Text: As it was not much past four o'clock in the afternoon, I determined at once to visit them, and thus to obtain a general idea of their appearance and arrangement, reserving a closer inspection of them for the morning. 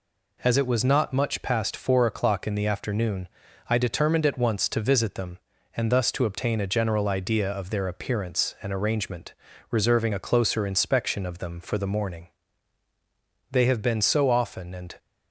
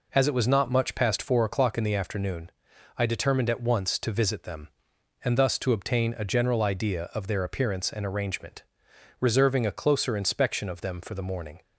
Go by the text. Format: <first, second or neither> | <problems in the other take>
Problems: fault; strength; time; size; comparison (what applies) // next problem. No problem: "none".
second | goes on to say "They have been so often and"; from 13.5 s on; 1.4 s long